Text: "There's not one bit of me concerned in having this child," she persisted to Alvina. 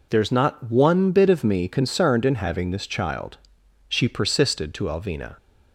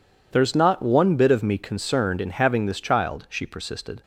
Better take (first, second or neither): first